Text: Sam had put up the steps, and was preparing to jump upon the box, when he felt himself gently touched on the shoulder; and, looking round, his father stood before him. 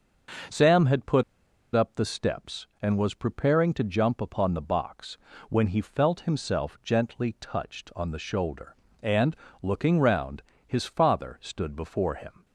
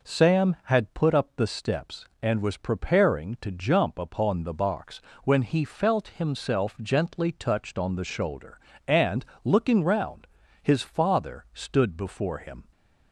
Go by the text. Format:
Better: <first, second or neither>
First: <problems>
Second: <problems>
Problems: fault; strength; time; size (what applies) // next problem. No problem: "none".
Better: second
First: pauses between "put" and "up"; noticeable; at 1.2 s; 0.51 s long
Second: none